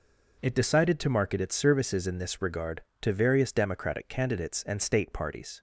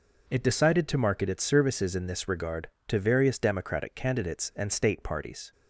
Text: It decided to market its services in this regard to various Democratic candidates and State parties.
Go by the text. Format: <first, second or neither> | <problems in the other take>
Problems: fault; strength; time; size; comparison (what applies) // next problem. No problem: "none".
neither | none